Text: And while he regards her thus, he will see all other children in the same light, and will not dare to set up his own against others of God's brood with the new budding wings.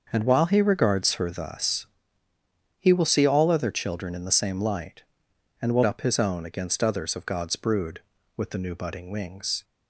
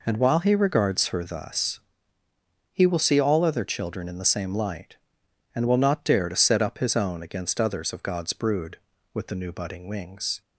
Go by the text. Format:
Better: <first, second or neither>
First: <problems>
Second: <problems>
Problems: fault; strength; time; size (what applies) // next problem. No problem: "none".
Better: second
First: starts louder than the rest; until 1.1 s; 6.5 dB // skips "not dare to set"; at 5.8 s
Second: none